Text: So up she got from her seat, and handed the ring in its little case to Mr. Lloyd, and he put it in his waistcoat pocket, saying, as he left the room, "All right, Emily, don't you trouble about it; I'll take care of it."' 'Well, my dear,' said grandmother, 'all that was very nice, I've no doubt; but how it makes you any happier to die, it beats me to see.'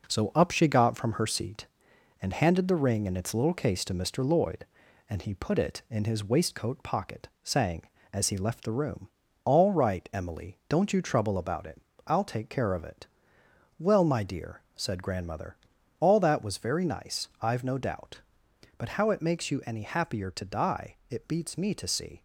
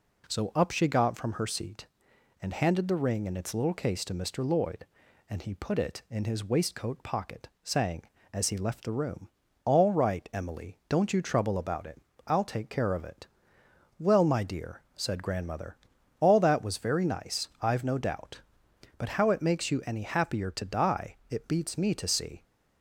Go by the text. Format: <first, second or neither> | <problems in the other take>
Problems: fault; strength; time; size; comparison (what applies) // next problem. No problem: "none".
second | gets quieter; noticeable; throughout; 5 dB